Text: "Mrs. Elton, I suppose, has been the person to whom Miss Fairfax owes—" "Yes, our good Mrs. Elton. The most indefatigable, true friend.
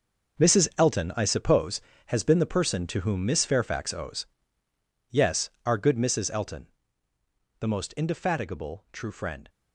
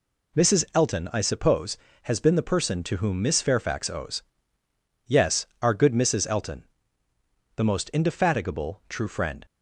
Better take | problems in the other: second | gets quieter; strong; throughout; 12.5 dB

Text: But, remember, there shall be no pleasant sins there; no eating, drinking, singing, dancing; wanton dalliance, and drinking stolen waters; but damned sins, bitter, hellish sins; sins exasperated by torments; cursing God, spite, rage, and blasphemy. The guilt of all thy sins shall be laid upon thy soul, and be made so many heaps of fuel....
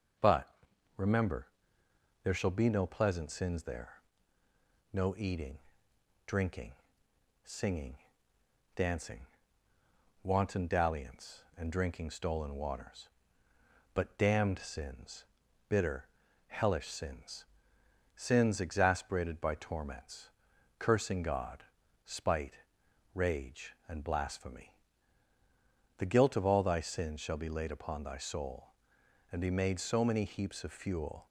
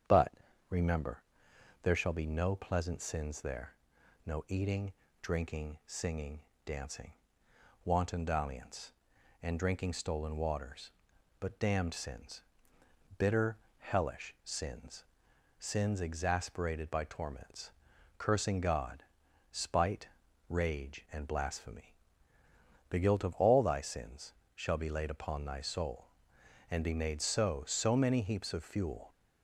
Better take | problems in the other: first | starts louder than the rest; strong; until 2.0 s; 8 dB // pauses between "sins" and "shall"; slight; at 24.3 s; 0.22 s long // says "so" twice; at 27.6 s

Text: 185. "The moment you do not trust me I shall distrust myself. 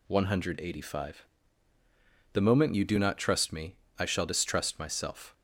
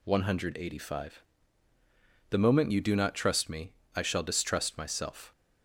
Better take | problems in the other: neither | pauses between "me" and "I"; slight; the same in both

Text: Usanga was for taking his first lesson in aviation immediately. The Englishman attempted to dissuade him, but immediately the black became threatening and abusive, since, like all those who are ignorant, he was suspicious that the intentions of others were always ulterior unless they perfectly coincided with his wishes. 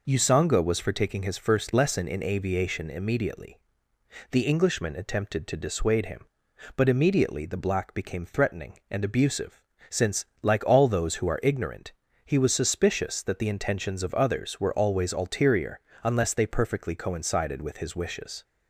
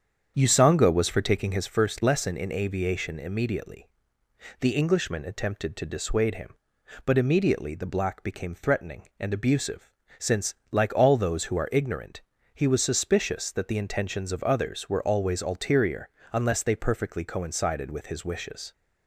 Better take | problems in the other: first | starts louder than the rest; strong; until 1.8 s; 7.5 dB // pauses between "ulterior" and "unless"; slight; at 16.0 s; 0.24 s long; slight in the first

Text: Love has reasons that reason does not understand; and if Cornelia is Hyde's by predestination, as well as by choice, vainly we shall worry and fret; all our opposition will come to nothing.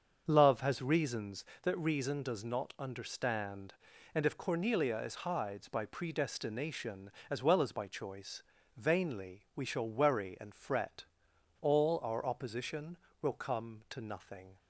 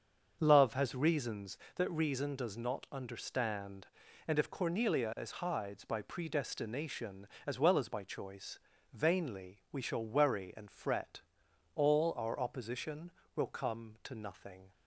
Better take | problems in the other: neither | starts louder than the rest; the same in both

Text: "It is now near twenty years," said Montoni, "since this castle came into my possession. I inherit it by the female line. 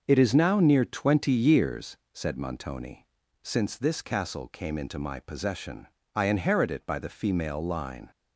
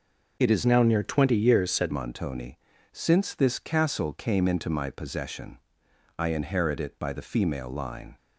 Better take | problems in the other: first | changes voice from "now" to "said"; from 0.6 to 1.9 s; 1.3 s long

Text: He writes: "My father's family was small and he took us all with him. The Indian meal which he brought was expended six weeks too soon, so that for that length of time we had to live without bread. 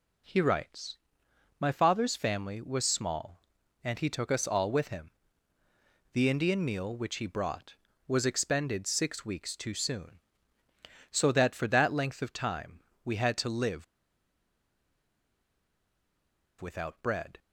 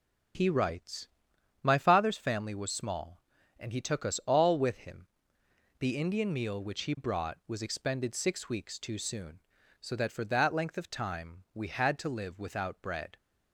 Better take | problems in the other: second | pauses between "time" and "we"; slight; at 12.8 s; 0.24 s long // pauses between "live" and "without"; strong; at 13.8 s; 2.7 s long

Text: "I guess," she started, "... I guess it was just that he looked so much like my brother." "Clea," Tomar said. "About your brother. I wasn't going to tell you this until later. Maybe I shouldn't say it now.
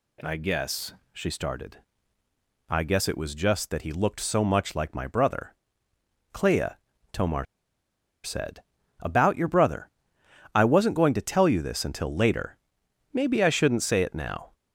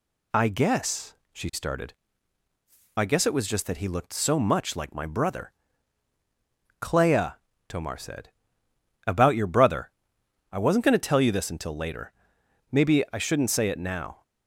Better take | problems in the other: second | pauses between "Tomar" and "said"; noticeable; at 7.4 s; 0.78 s long

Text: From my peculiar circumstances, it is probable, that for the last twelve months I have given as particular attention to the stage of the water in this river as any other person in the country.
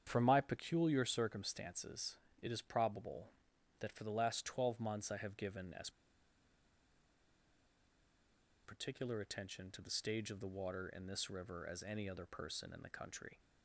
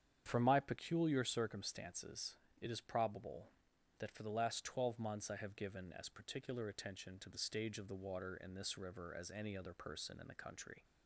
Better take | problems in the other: second | starts louder than the rest; strong; until 1.0 s; 8.5 dB; strong in the second // pauses between "as" and "particular"; strong; at 5.8 s; 2.7 s long

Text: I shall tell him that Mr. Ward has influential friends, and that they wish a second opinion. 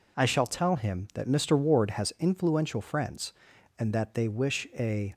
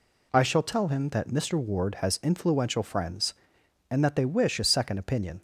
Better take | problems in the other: second | stops before "second opinion"; at 5.1 s

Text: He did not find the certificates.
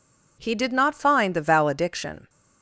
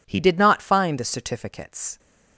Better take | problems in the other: second | says "valediction" for "certificates"; at 1.4 s

